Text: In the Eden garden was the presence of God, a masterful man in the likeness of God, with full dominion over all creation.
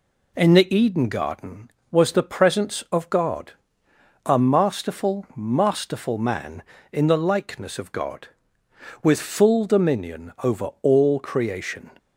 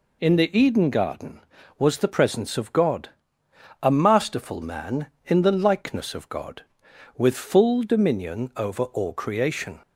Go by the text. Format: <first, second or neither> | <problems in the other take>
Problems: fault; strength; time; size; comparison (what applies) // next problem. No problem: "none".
second | says "masterful" twice; at 5.3 s